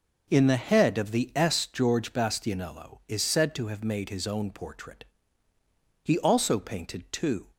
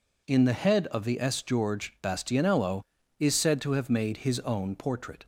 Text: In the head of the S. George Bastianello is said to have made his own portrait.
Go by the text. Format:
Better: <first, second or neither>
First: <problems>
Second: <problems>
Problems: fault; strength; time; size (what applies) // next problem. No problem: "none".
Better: second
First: goes on to say "He also painted two"; from 6.0 s on; 1.4 s long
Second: none